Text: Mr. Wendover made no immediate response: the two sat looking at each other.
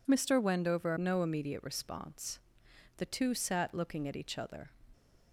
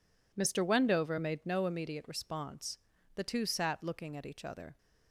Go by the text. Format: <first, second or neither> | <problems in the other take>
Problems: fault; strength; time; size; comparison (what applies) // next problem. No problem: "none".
second | skips "made"; at 0.9 s